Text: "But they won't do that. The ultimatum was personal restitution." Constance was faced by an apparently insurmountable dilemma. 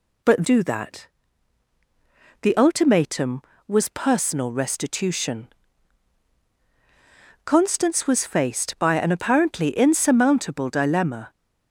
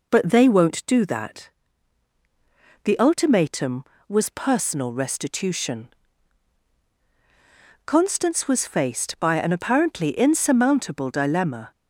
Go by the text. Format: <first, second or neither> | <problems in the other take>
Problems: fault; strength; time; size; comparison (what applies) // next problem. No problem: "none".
second | skips "they won't"; at 0.4 s